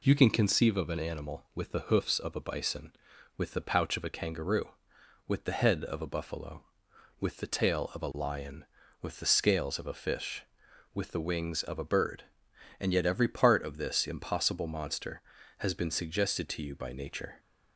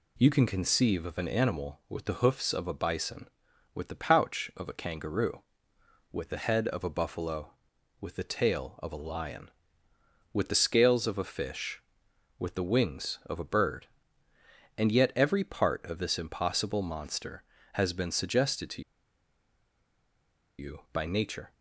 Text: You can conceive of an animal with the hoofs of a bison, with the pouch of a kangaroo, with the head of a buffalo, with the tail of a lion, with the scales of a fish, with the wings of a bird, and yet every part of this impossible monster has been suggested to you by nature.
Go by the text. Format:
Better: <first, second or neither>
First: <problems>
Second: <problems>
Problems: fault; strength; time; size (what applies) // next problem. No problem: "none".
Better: first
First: none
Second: pauses between "to" and "you"; strong; at 18.8 s; 1.7 s long